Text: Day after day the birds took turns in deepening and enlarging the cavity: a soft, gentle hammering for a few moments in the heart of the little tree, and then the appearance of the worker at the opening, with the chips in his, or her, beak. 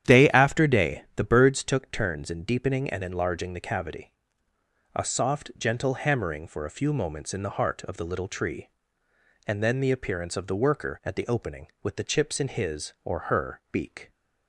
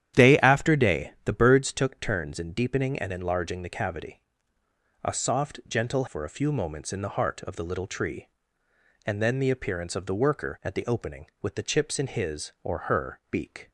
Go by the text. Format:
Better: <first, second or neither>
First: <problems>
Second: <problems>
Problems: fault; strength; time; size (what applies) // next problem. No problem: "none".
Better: first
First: starts louder than the rest; strong; until 1.1 s; 10 dB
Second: starts louder than the rest; strong; until 1.2 s; 10.5 dB // skips "hammering"; at 6.0 s